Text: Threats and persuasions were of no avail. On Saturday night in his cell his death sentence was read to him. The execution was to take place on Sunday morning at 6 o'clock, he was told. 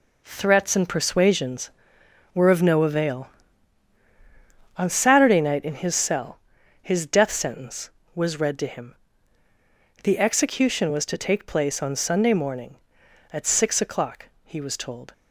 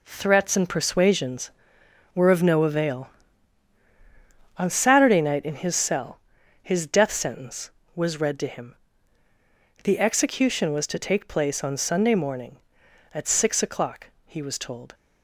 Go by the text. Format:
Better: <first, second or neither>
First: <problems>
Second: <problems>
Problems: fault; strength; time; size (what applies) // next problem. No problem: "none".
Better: neither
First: pauses between "cell" and "his"; at 6.3 s; 0.42 s long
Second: pauses between "cell" and "his"; at 6.1 s; 0.42 s long